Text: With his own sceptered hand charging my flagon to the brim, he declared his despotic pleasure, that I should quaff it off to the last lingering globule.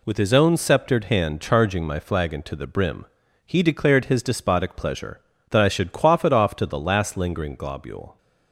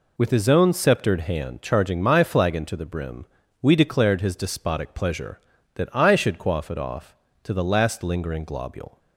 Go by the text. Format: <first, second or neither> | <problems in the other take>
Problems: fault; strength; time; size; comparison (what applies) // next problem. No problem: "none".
first | says "we" for "he"; at 3.6 s